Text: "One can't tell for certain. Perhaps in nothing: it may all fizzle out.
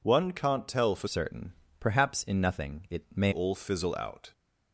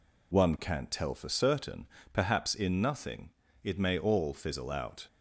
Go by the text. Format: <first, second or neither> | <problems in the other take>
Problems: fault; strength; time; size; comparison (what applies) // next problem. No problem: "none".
second | changes voice from "certain" to "may"; from 1.0 to 3.3 s; 2.3 s long